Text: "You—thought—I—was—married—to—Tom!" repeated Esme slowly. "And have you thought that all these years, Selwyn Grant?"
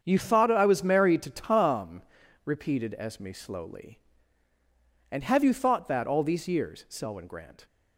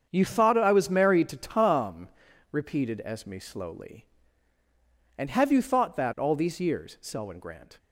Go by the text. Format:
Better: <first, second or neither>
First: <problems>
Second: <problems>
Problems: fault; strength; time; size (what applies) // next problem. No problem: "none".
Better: neither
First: starts louder than the rest; strong; until 1.0 s; 7 dB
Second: starts louder than the rest; strong; until 1.1 s; 7 dB